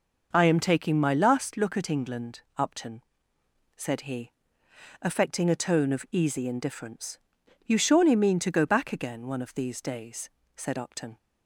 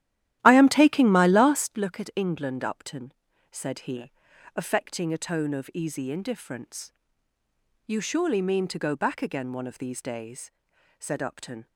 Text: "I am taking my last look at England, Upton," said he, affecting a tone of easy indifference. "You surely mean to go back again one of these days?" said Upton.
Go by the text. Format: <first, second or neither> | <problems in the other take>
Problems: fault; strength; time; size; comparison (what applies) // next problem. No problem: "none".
first | starts louder than the rest; strong; until 1.7 s; 13 dB